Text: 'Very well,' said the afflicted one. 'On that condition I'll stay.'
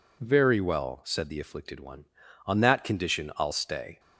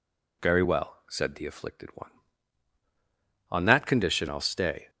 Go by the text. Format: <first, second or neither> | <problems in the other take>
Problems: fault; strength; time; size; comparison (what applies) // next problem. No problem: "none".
neither | none